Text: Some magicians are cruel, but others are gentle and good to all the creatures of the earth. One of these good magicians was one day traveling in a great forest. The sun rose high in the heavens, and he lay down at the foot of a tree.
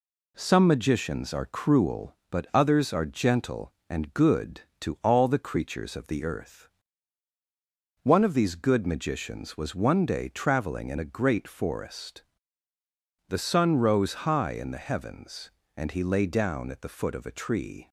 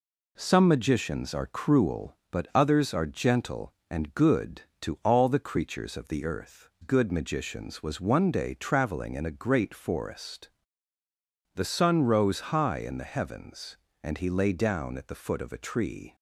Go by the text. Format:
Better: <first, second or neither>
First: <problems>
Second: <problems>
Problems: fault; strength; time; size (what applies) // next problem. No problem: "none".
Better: first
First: none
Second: skips "One of these"; at 6.7 s